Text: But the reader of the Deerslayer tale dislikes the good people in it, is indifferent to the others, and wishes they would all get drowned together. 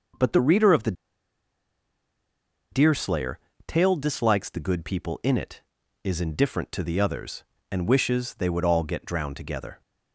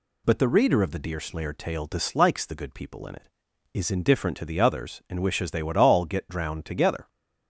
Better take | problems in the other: second | pauses between "the" and "Deerslayer"; strong; at 0.9 s; 1.7 s long // pauses between "Deerslayer" and "tale"; slight; at 3.3 s; 0.28 s long

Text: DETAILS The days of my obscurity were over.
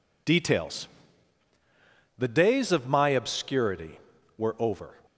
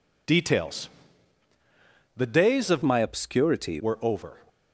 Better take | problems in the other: first | pauses between "DETAILS" and "The"; strong; at 0.8 s; 1.2 s long; strong in the first // changes voice from "my" to "obscurity"; from 2.8 to 3.8 s; 1.0 s long

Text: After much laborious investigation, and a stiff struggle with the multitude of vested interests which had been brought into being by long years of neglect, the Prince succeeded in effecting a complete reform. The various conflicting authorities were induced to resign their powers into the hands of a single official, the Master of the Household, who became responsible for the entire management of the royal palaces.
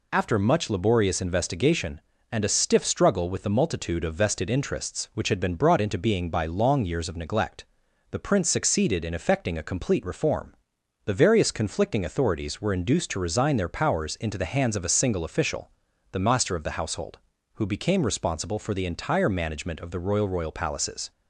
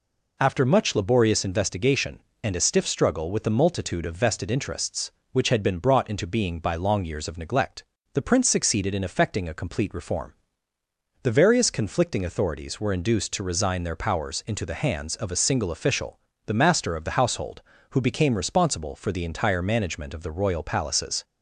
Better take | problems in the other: second | says "royal" twice; at 20.2 s

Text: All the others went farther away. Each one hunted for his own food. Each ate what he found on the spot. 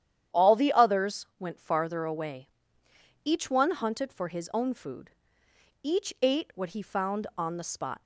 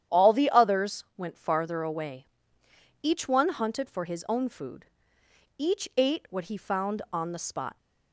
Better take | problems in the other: neither | starts louder than the rest; strong; the same in both

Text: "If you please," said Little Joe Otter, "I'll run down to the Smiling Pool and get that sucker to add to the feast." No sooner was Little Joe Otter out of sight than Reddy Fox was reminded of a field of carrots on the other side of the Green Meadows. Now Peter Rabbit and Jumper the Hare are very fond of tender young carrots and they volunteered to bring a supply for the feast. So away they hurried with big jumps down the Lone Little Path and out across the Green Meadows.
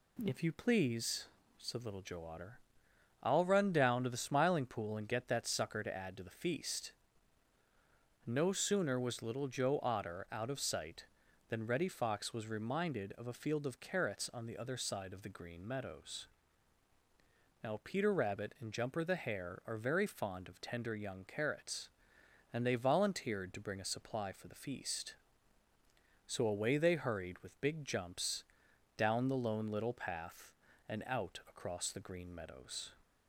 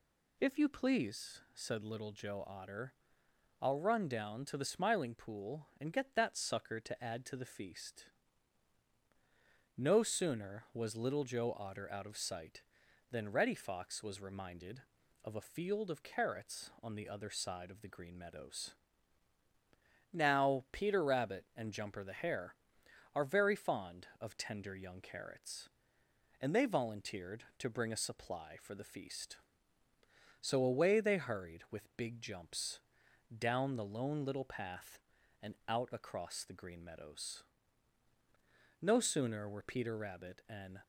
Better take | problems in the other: first | pauses between "jumps" and "down"; noticeable; at 32.7 s; 0.56 s long; noticeable in the first // goes on to say "No sooner were Peter Rabbit and"; strong; from 38.7 s on; 2.0 s long

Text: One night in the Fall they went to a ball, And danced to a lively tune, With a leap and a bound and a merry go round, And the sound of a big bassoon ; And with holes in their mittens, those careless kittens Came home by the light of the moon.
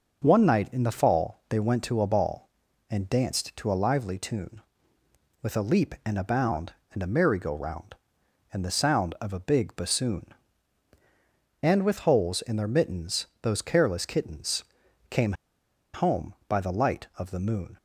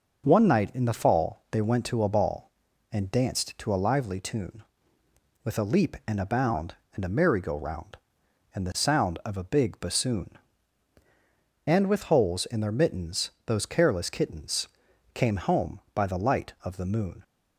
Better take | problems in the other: second | pauses between "kittens" and "Came"; noticeable; at 14.6 s; 0.46 s long; noticeable in the second // pauses between "Came" and "home"; noticeable; at 15.3 s; 0.60 s long

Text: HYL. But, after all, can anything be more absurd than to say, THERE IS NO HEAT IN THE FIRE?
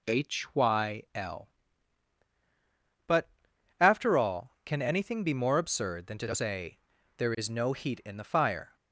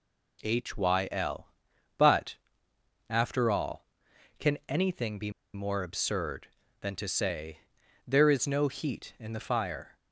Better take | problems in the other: first | pauses between "be" and "more"; slight; at 5.2 s; 0.24 s long

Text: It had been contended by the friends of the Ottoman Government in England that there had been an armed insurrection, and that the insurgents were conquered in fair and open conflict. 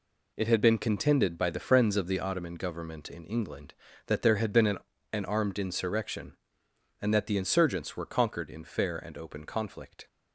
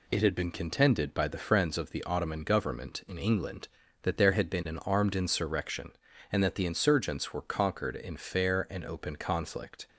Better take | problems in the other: second | says "an" twice; at 5.1 s

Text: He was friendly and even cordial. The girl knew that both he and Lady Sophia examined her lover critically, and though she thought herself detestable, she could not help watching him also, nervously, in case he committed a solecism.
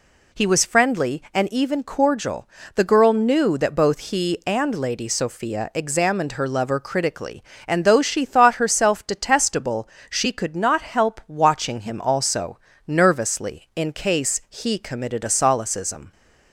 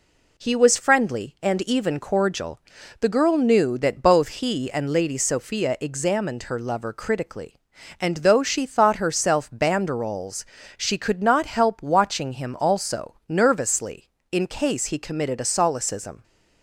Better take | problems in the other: first | says "banderoles" for "detestable"; at 9.5 s

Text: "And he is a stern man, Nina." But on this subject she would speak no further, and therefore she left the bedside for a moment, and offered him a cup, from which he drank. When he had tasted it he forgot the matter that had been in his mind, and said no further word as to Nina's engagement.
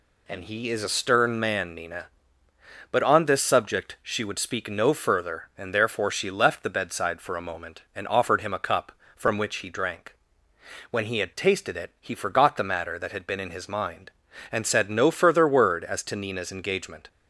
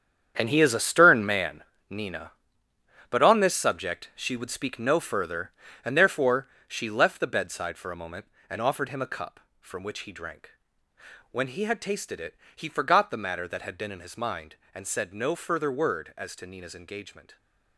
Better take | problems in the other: first | gets quieter; strong; throughout; 11 dB // pauses between "therefore" and "she"; slight; at 6.4 s; 0.22 s long // pauses between "it" and "he"; slight; at 12.3 s; 0.22 s long

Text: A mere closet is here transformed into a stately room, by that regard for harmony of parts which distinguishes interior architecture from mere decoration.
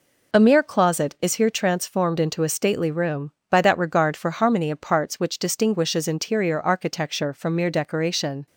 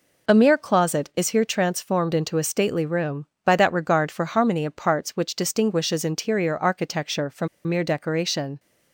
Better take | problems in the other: first | pauses between "from" and "mere"; slight; at 7.4 s; 0.19 s long

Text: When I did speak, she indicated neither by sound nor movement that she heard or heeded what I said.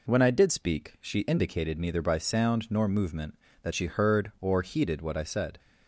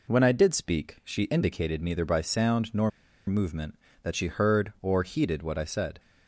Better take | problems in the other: first | pauses between "nor" and "movement"; at 2.9 s; 0.37 s long

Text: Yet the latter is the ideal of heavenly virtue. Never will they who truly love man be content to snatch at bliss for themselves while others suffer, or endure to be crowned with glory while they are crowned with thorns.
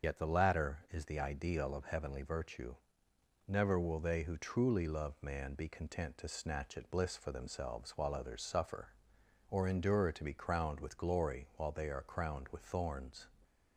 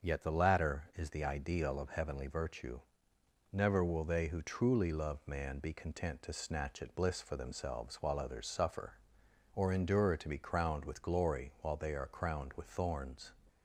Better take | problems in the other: second | loses the start of "Yet"; at 0.0 s; 60 ms // starts louder than the rest; until 1.1 s; 6.5 dB; also in the second

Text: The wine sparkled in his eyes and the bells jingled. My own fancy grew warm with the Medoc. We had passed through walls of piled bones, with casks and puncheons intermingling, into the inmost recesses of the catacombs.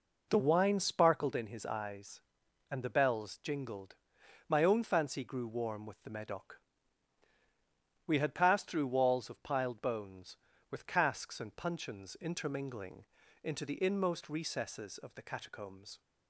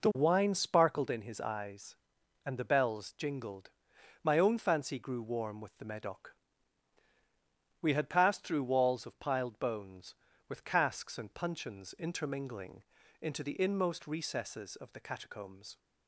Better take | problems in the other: neither | none

